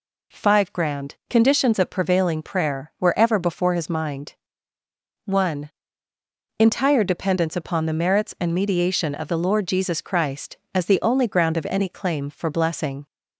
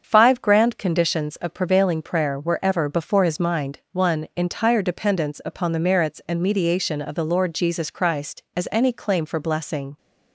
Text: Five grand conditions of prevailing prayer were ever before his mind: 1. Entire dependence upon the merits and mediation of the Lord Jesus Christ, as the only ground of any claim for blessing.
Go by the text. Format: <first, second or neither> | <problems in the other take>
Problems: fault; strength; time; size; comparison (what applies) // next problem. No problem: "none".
first | starts louder than the rest; until 1.0 s; 7 dB // skips "the only ground of"; at 8.6 s